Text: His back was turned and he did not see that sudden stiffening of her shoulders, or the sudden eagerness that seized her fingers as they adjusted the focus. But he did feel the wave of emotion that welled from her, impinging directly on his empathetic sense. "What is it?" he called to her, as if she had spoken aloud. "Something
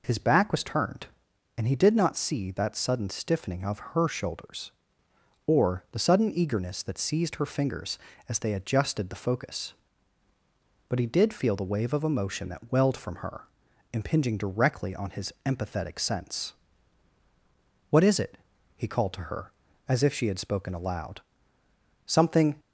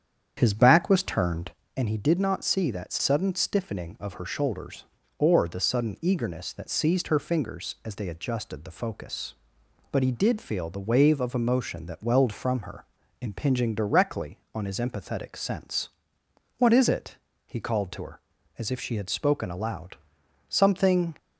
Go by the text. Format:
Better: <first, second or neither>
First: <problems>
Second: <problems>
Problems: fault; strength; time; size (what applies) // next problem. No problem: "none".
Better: first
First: none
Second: starts louder than the rest; strong; until 1.6 s; 8.5 dB